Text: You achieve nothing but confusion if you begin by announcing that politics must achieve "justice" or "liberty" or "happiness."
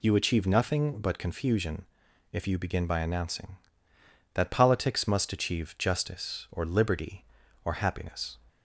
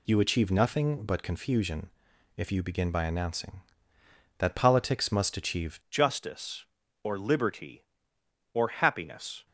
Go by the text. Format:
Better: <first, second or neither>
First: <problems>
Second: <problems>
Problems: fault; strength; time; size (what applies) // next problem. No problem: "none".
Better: first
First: pauses between "confusion" and "if"; noticeable; at 1.8 s; 0.48 s long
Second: pauses between "confusion" and "if"; noticeable; at 1.8 s; 0.48 s long // changes voice at "justice"; from 5.8 s on; 3.6 s long